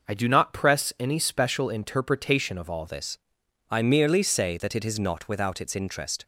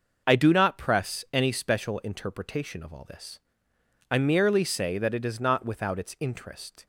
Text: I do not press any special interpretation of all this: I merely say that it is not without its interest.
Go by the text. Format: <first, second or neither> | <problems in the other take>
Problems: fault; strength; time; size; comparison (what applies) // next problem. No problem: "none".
second | changes voice at "this"; from 2.8 s on; 3.4 s long